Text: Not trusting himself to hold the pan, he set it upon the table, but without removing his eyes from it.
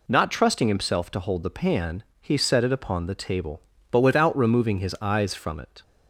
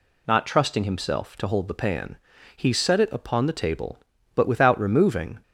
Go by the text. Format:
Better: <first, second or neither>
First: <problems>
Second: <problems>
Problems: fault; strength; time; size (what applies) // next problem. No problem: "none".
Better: first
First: none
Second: stops before "his eyes from it"; at 5.4 s